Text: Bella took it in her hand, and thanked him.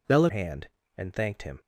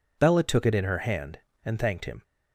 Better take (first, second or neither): second